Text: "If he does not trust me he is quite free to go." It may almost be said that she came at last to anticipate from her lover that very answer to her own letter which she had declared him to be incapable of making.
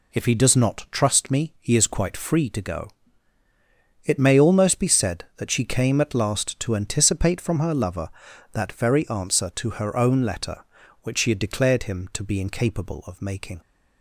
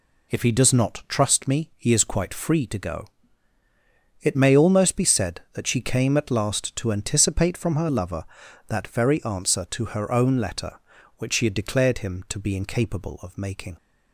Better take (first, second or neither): neither